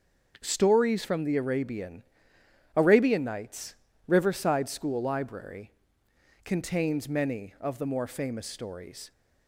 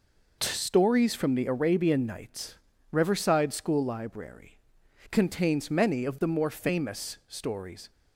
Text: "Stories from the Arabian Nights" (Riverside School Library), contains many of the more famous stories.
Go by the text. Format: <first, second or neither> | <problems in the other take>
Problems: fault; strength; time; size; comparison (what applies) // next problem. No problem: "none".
second | starts louder than the rest; until 1.4 s; 6.5 dB // says "Arabian" twice; at 2.7 s